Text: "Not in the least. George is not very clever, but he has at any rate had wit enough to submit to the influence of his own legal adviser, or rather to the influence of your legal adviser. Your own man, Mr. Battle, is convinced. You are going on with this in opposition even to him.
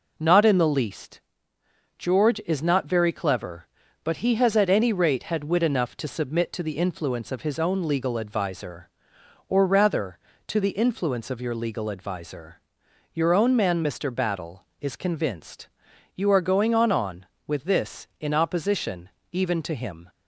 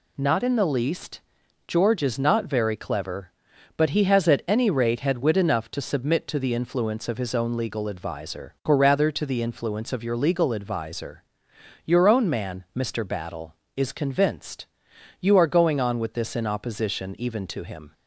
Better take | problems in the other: second | says "on" twice; at 16.9 s // pauses between "opposition" and "even"; slight; at 19.1 s; 0.22 s long

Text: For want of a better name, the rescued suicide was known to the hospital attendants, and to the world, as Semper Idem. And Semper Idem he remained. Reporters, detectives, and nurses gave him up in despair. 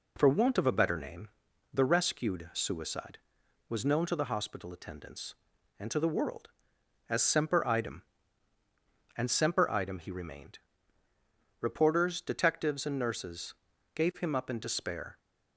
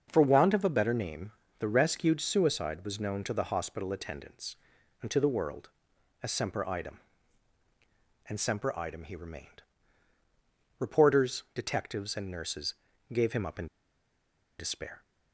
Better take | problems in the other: first | starts louder than the rest; until 1.1 s; 6.5 dB // pauses between "nurses" and "gave"; at 12.7 s; 0.40 s long; also in the first // pauses between "in" and "despair"; noticeable; at 13.6 s; 0.92 s long

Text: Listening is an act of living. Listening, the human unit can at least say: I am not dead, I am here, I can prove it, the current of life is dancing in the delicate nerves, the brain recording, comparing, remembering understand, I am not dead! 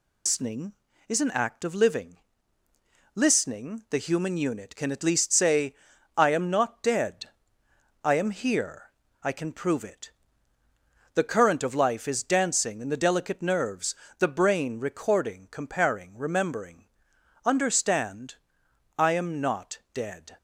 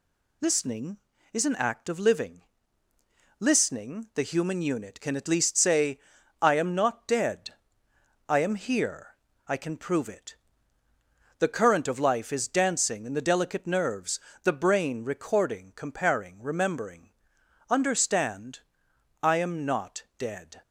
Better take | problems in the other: second | loses the start of "Listening"; at 0.2 s; 85 ms // pauses between "remembering" and "understand"; noticeable; at 16.8 s; 0.58 s long; noticeable in the second

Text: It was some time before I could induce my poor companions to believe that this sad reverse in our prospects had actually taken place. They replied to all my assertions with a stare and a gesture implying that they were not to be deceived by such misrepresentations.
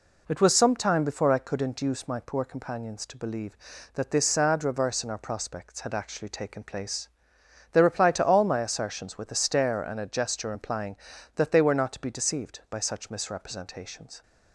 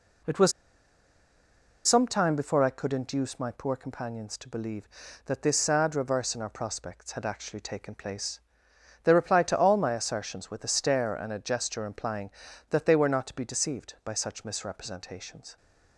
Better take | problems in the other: first | pauses between "was" and "some"; strong; at 0.5 s; 1.3 s long

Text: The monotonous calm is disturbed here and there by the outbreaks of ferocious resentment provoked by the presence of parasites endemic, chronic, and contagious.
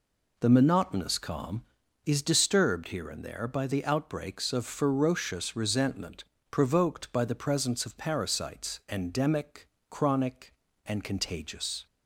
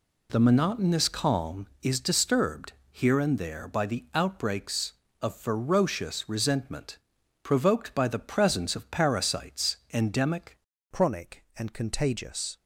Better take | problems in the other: first | pauses between "disturbed" and "here"; slight; at 2.7 s; 0.22 s long // pauses between "resentment" and "provoked"; at 6.9 s; 0.44 s long; slight in the first // pauses between "parasites" and "endemic"; slight; at 9.7 s; 0.18 s long // changes voice at "chronic"; from 10.9 s on; 1.6 s long

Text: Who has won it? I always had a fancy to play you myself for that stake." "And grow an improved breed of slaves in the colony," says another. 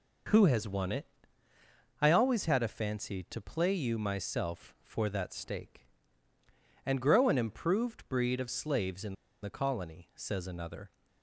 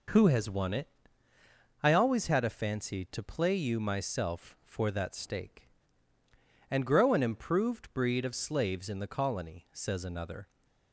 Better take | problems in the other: second | pauses between "in" and "the"; slight; at 9.1 s; 0.29 s long

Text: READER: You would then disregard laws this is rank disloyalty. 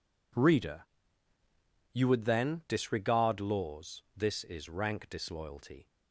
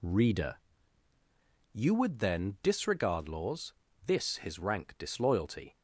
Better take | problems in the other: first | pauses between "laws" and "this"; slight; at 3.7 s; 0.32 s long // says "his" for "is"; at 4.3 s

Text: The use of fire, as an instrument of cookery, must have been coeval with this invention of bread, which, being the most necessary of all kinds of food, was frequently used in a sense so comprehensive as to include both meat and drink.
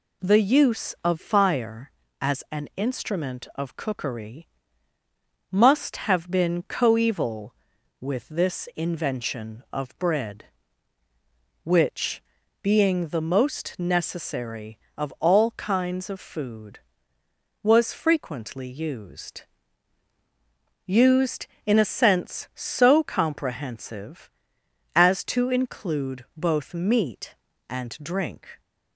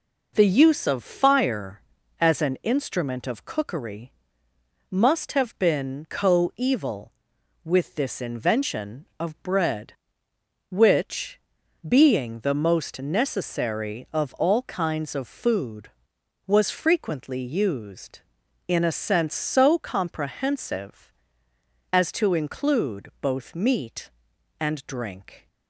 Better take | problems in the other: second | says "used" twice; at 20.8 s

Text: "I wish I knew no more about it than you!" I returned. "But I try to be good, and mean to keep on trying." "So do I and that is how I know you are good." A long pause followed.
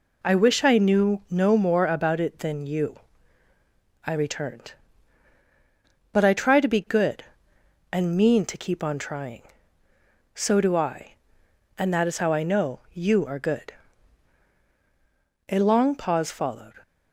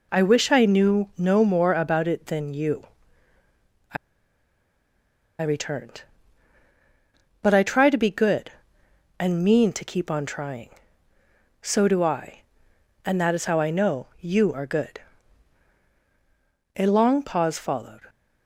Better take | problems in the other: first | pauses between "I" and "returned"; strong; at 3.9 s; 1.4 s long

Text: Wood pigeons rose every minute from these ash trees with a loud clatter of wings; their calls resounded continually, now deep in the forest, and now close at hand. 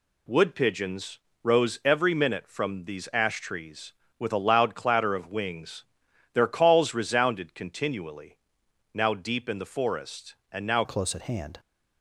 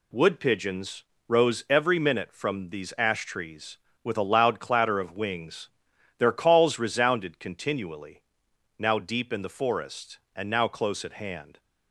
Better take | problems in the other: second | pauses between "pigeons" and "rose"; slight; at 1.1 s; 0.22 s long; slight in the second // changes voice at "close"; from 10.8 s on; 0.7 s long

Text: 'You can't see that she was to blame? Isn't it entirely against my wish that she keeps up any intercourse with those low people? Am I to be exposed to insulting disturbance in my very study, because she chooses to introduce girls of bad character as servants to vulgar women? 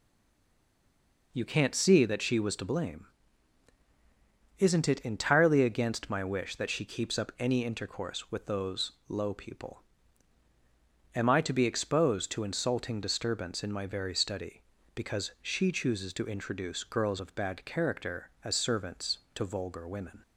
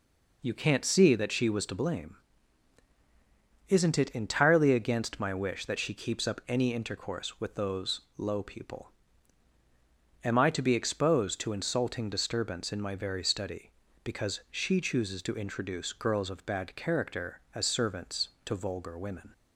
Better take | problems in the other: second | stays silent before the first word; noticeable; until 1.3 s; 1.3 s long // pauses between "those" and "low"; slight; at 8.9 s; 0.16 s long; slight in the second

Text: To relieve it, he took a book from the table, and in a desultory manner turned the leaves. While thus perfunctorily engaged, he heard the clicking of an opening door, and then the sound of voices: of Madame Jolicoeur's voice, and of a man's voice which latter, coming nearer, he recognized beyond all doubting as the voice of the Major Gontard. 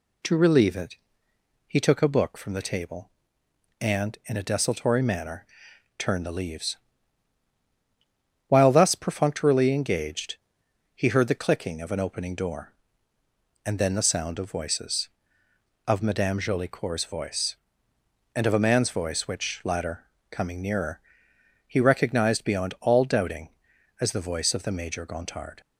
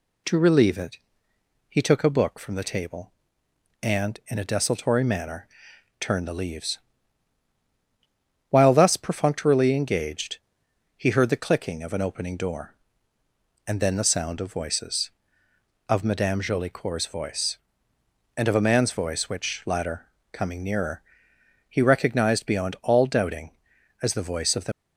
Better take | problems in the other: first | pauses between "manner" and "turned"; noticeable; at 5.4 s; 0.54 s long; noticeable in the first // stops before "Major Gontard"; at 24.7 s

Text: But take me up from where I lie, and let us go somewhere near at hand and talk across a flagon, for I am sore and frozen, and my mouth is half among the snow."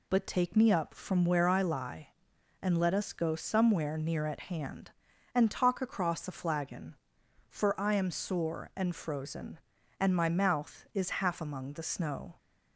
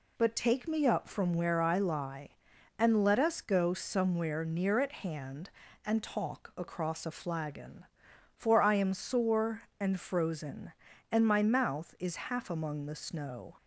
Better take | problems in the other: neither | none

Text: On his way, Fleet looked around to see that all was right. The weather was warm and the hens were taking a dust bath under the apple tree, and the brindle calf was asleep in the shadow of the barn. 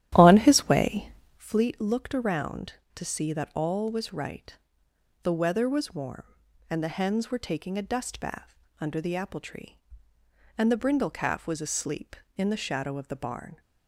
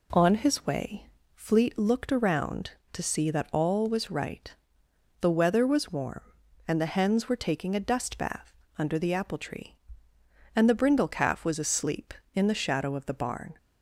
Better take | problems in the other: second | starts louder than the rest; strong; until 1.5 s; 12 dB // pauses between "bath" and "under"; slight; at 8.5 s; 0.24 s long; slight in the second

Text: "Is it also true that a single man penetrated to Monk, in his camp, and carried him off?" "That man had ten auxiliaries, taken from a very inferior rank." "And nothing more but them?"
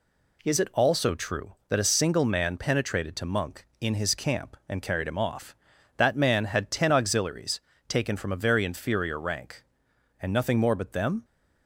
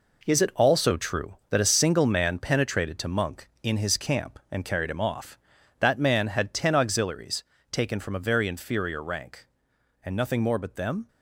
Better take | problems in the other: first | gets quieter; strong; throughout; 8.5 dB

